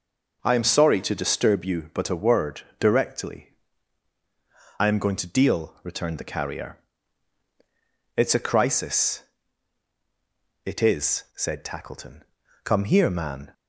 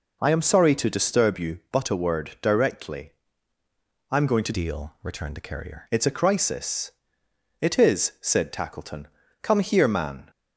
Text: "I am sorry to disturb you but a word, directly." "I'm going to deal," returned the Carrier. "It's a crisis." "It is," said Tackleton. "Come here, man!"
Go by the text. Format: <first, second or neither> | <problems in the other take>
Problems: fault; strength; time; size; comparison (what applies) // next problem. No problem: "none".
first | changes voice from "deal" to "Carrier"; from 4.5 to 5.8 s; 1.3 s long